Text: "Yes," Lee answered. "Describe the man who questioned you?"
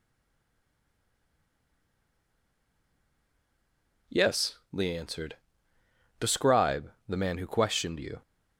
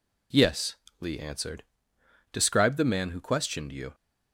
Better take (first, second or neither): second